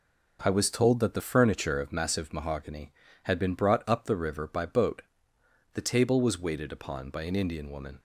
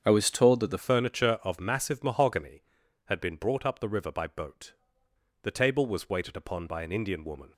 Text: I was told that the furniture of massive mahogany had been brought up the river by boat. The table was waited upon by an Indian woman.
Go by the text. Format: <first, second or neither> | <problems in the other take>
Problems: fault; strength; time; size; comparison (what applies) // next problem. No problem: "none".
first | starts louder than the rest; strong; until 1.0 s; 7.5 dB // changes voice at "furniture"; from 0.7 s on; 6.8 s long